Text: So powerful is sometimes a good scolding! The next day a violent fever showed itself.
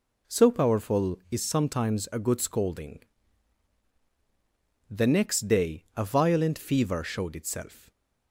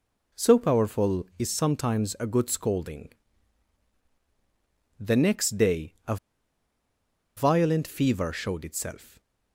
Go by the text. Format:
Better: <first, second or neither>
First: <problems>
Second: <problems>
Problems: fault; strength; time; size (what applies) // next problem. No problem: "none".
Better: first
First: stays silent after the last word; slight; from 7.7 s on; 0.6 s long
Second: pauses between "a" and "violent"; at 6.1 s; 1.2 s long // stays silent after the last word; slight; from 9.0 s on; 0.5 s long